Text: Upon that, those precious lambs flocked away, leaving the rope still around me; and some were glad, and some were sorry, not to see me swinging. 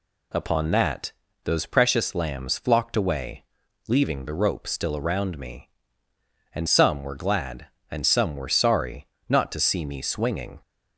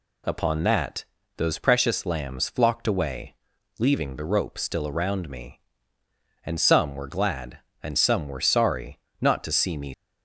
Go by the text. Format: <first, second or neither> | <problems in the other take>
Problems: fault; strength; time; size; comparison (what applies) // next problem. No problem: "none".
first | stops before "swinging"; at 9.9 s